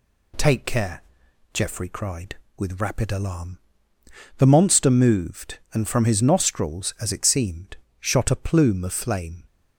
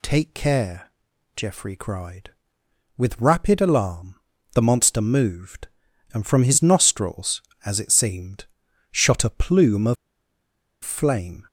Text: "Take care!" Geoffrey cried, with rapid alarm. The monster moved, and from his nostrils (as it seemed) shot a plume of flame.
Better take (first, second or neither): first